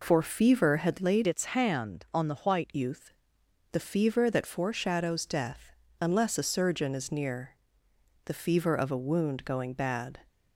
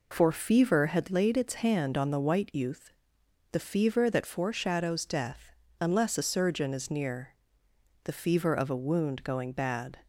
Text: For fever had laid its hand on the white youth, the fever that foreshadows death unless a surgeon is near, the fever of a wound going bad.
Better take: second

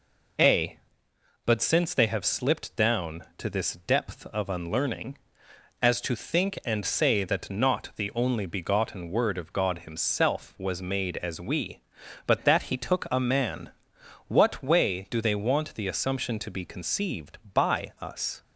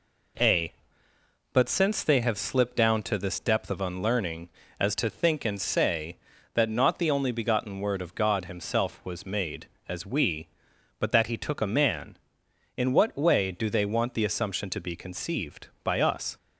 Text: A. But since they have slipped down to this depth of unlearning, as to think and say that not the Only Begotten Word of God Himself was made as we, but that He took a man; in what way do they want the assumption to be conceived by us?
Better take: second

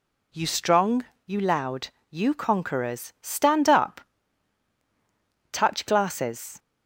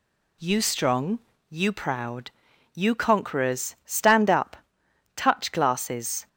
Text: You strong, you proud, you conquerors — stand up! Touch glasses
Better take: second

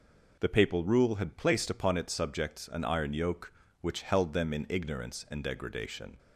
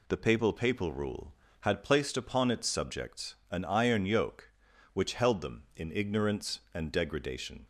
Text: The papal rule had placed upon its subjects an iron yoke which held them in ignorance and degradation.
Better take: first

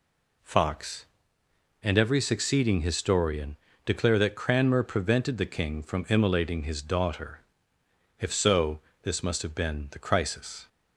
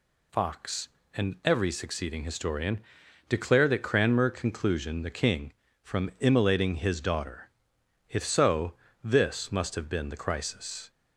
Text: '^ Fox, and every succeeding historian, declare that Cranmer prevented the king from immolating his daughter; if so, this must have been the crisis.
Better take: first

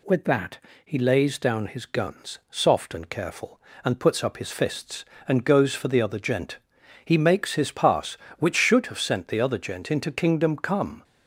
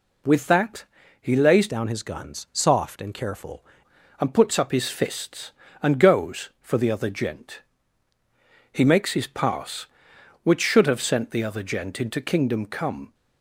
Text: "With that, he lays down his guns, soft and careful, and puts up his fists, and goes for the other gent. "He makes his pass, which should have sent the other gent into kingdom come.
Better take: first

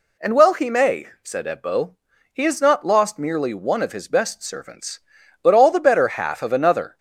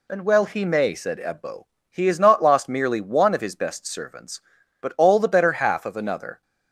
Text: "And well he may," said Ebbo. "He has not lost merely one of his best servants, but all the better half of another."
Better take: neither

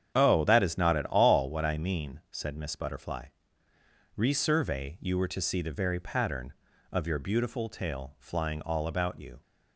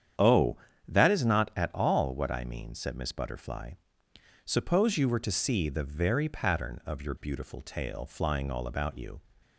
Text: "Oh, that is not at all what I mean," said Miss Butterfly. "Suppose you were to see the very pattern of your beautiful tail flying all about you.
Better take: second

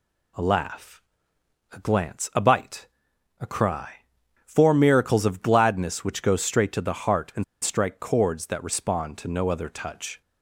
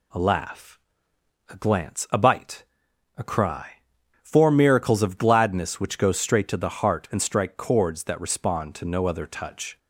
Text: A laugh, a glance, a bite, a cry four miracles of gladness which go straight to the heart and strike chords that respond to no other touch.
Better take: second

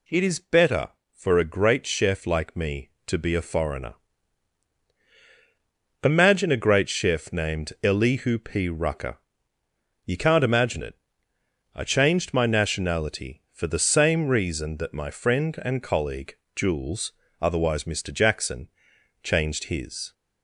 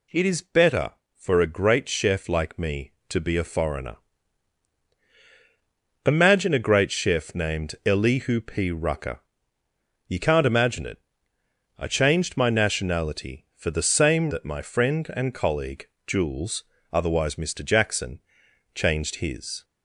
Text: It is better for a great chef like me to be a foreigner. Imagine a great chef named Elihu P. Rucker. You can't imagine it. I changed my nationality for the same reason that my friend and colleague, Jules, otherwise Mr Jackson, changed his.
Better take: first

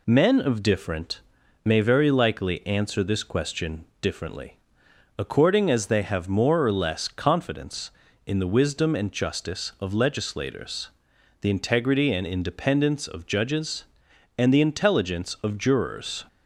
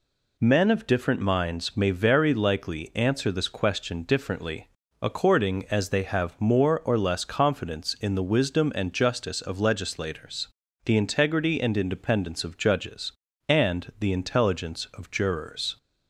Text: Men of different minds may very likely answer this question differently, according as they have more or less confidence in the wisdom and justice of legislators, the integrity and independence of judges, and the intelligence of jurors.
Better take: second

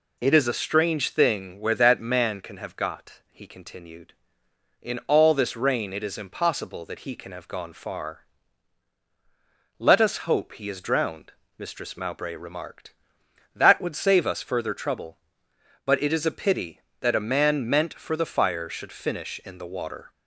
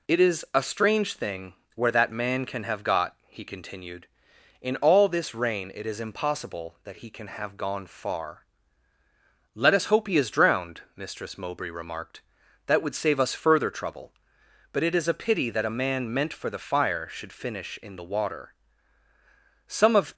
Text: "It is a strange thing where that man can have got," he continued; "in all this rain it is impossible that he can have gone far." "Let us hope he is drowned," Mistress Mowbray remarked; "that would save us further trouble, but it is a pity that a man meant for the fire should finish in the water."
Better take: first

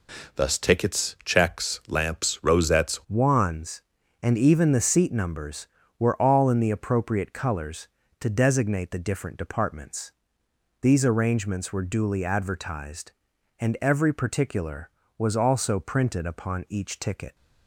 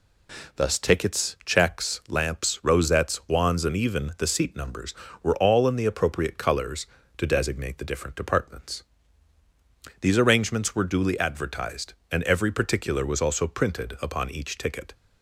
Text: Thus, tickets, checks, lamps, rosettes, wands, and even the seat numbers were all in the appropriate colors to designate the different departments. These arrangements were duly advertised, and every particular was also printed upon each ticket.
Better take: second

